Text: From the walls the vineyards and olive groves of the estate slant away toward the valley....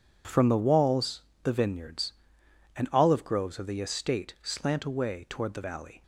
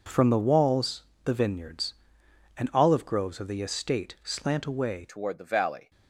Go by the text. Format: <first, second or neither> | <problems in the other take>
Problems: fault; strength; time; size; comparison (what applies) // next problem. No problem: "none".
first | pauses between "walls" and "the"; slight; at 1.0 s; 0.22 s long; slight in the first // changes voice at "toward"; from 5.0 s on; 0.9 s long